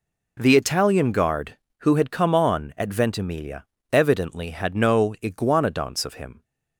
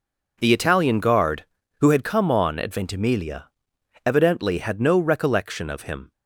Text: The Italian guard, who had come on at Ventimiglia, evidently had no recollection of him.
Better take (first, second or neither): second